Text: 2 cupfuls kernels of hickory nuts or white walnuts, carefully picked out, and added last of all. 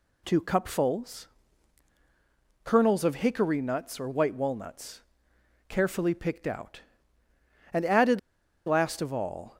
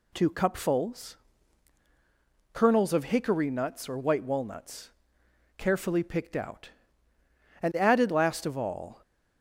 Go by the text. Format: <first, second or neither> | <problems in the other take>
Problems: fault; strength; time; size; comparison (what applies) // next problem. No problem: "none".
second | pauses between "cupfuls" and "kernels"; strong; at 1.2 s; 1.3 s long; strong in the second // pauses between "added" and "last"; noticeable; at 8.1 s; 0.47 s long